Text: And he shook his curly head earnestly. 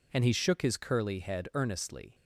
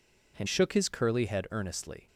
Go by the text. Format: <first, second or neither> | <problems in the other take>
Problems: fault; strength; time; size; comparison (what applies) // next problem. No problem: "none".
first | skips "he"; at 0.4 s